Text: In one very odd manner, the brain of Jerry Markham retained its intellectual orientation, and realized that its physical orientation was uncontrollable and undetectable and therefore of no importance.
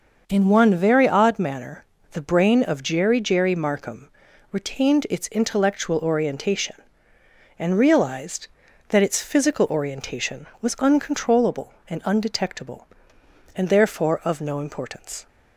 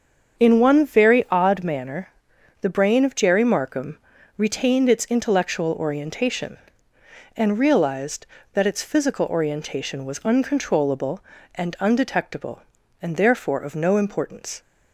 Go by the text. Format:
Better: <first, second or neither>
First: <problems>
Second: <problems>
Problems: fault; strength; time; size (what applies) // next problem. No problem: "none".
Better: second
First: starts louder than the rest; noticeable; until 1.2 s; 6 dB // says "Jerry" twice; at 3.2 s // pauses between "Markham" and "retained"; at 4.0 s; 0.42 s long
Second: starts louder than the rest; until 1.4 s; 7 dB // pauses between "Markham" and "retained"; at 3.9 s; 0.40 s long